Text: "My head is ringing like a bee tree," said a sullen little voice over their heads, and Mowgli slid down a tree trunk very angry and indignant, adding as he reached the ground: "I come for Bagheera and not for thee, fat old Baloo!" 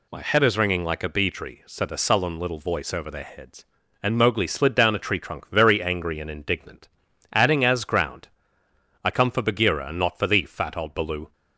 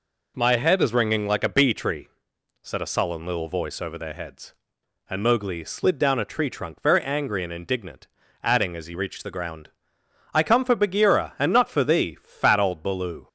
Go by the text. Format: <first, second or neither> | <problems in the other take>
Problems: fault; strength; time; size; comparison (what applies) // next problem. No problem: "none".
second | skips "he reached the"; at 7.8 s